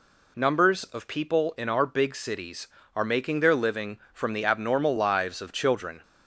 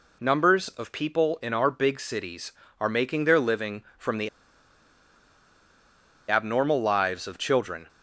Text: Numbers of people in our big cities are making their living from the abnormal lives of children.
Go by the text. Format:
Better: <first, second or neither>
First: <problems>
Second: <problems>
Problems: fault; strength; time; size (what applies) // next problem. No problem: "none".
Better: first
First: none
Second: pauses between "the" and "abnormal"; strong; at 4.2 s; 2.0 s long